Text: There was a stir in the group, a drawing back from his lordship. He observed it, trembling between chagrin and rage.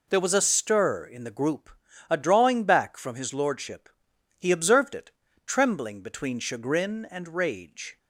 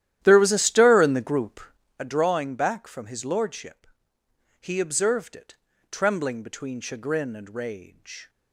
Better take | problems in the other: first | starts louder than the rest; strong; until 1.9 s; 12 dB

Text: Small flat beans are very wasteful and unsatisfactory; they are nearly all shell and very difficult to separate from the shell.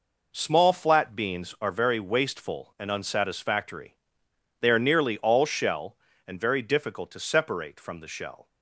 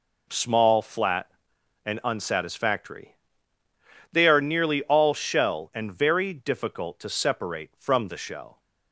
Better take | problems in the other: first | skips "beans are very wasteful"; at 1.5 s

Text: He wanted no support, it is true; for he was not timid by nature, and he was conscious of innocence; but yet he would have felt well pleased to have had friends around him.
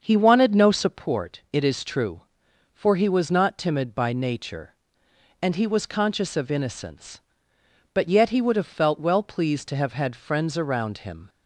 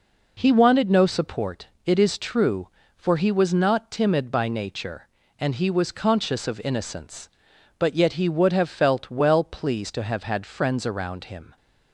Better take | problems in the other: second | starts louder than the rest; until 1.1 s; 6.5 dB

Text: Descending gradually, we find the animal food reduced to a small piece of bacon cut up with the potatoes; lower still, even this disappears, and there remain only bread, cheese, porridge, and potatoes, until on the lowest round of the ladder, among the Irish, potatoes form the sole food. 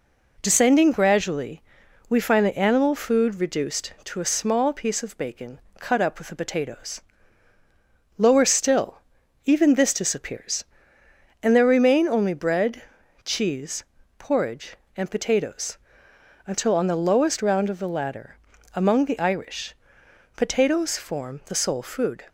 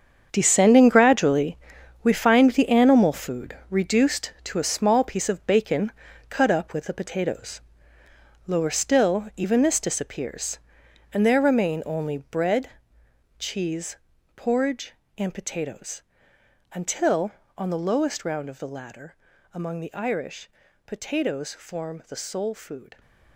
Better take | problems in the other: first | gets quieter; strong; throughout; 12.5 dB // pauses between "bacon" and "cut"; at 5.8 s; 0.40 s long; slight in the first

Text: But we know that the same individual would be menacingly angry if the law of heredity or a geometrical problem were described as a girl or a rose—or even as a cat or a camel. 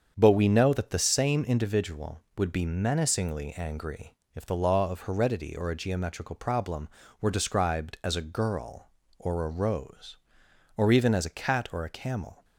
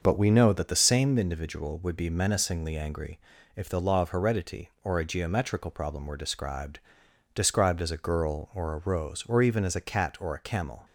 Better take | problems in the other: first | starts louder than the rest; until 1.0 s; 6.5 dB; strong in the first // pauses between "angry" and "if"; slight; at 3.1 s; 0.36 s long; slight in the first // says "described" twice; at 7.3 s

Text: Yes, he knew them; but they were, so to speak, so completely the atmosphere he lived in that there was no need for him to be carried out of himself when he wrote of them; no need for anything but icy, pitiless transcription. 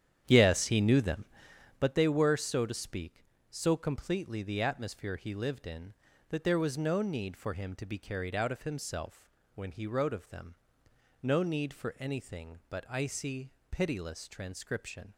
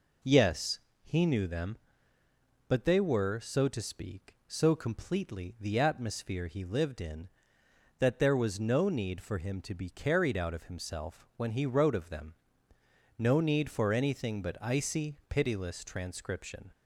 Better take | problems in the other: second | starts louder than the rest; strong; until 1.9 s; 9.5 dB // pauses between "himself" and "when"; slight; at 9.2 s; 0.26 s long

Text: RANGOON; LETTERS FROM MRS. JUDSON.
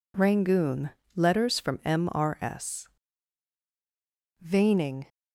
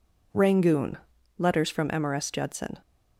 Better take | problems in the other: second | says "Veining" for "JUDSON"; at 4.3 s

